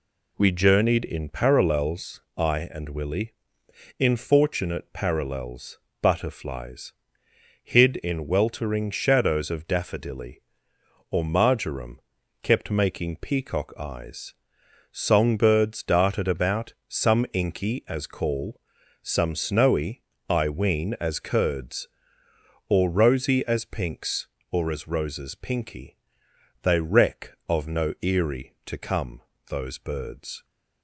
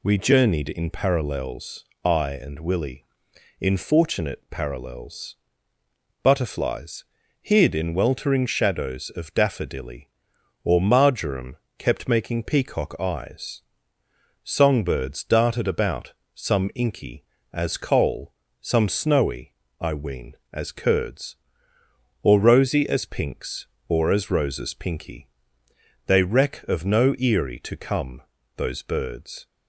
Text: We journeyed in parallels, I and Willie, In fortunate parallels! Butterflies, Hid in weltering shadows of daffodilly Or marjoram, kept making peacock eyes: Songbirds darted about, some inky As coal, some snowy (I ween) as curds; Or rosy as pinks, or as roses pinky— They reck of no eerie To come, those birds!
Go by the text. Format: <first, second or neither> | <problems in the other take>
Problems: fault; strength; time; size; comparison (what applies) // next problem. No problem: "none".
second | says "call" for "coal"; at 18.0 s